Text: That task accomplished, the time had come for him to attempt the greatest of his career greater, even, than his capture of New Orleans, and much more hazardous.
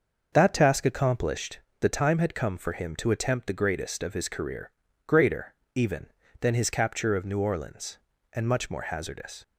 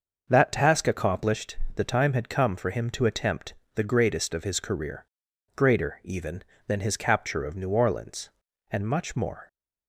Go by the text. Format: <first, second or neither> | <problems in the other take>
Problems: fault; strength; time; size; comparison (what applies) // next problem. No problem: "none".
first | starts louder than the rest; until 1.3 s; 6 dB; also in the first // pauses between "attempt" and "the"; slight; at 3.5 s; 0.22 s long // pauses between "career" and "greater"; noticeable; at 5.0 s; 0.50 s long; slight in the first // stops before "hazardous"; at 9.4 s